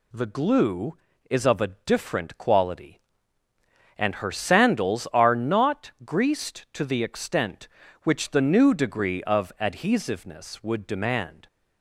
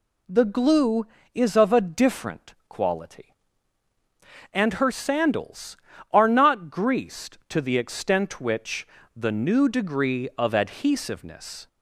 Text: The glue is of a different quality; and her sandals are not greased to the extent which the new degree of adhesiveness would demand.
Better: first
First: none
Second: pauses between "which" and "the"; slight; at 8.8 s; 0.28 s long // stops before "would demand"; at 11.6 s

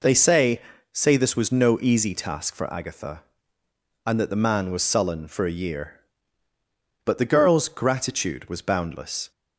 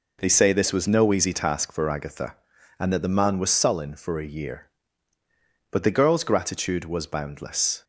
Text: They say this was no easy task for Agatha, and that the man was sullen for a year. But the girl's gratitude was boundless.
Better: second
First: says "say" twice; at 0.9 s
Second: none

